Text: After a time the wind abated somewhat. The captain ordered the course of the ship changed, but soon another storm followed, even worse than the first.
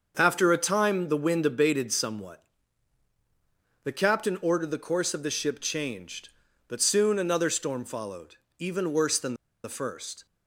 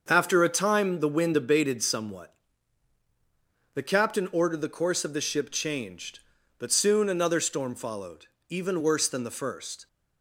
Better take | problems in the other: second | starts louder than the rest; until 1.1 s; 6.5 dB; also in the second // pauses between "than" and "the"; slight; at 9.3 s; 0.30 s long

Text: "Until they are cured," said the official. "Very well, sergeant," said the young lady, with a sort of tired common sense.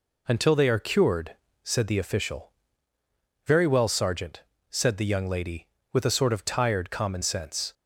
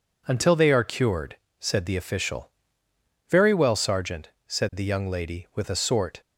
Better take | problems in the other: first | stops before "of tired common sense"; at 6.2 s

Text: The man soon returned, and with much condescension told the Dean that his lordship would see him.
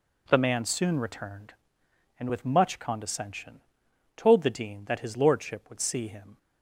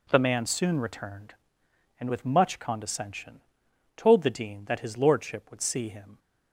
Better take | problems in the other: neither | pauses between "condescension" and "told"; noticeable; the same in both

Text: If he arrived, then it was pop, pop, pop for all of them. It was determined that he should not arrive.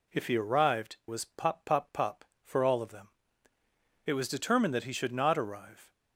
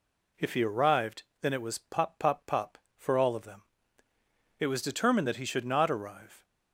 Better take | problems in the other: second | skips "then it"; at 1.0 s

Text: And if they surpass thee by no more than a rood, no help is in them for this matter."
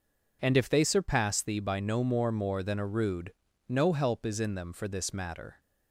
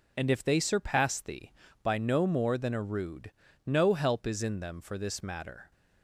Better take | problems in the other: second | says "more" twice; at 2.3 s

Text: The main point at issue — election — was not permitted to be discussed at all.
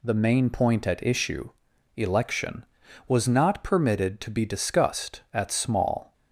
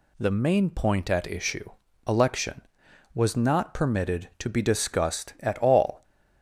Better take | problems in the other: second | says "small" for "all"; at 5.5 s

